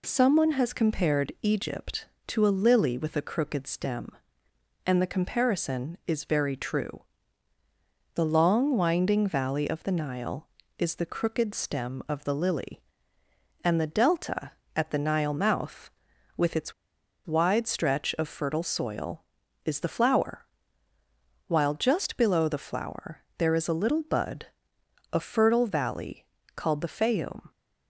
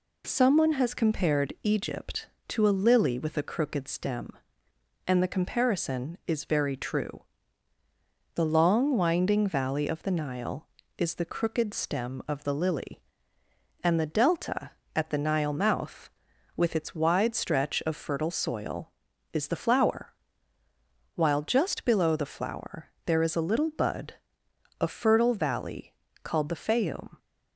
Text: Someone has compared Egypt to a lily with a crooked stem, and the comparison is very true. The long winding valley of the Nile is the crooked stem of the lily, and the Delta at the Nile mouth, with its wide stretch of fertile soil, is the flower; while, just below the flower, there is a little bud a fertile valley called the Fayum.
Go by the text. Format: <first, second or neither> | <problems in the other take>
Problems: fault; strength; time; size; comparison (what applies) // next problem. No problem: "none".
second | pauses between "its" and "wide"; noticeable; at 16.7 s; 0.53 s long // pauses between "bud" and "a"; noticeable; at 24.4 s; 0.66 s long; noticeable in the second // pauses between "valley" and "called"; slight; at 26.2 s; 0.30 s long; slight in the second